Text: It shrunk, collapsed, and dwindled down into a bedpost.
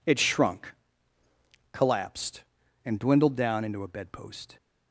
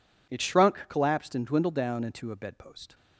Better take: neither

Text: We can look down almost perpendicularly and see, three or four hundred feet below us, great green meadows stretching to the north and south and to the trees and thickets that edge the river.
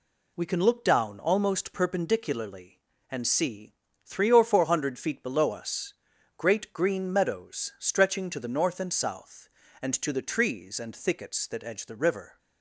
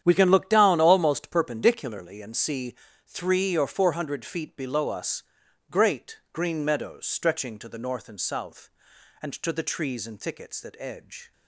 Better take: first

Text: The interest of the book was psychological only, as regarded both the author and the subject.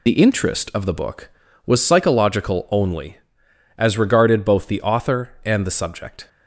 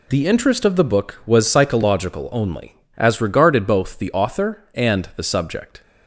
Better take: second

